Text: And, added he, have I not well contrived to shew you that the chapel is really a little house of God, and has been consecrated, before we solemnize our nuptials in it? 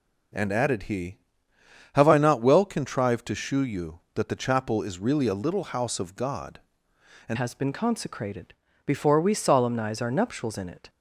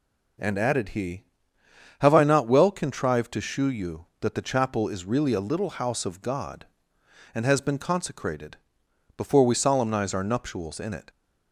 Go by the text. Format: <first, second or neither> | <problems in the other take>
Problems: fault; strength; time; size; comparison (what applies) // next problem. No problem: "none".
second | changes voice at "has"; from 7.3 s on; 3.5 s long